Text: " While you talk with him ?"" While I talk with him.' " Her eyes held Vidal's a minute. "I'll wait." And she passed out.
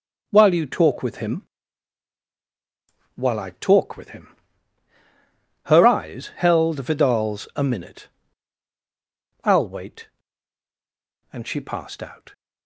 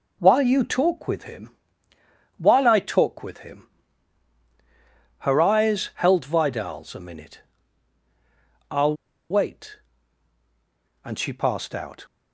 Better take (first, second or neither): first